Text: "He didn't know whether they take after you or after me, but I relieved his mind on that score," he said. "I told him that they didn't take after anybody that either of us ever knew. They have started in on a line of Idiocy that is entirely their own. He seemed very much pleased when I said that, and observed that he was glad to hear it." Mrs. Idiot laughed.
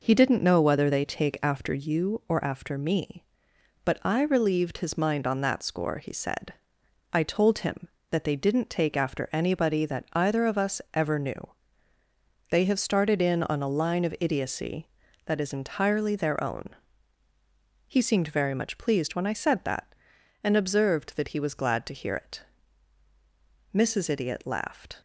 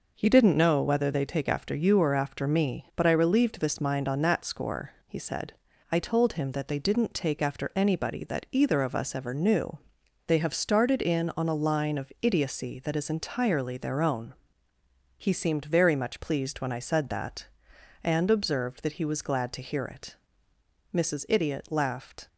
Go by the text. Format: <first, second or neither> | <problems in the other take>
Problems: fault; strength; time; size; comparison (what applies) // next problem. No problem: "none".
first | says "this" for "his"; at 3.5 s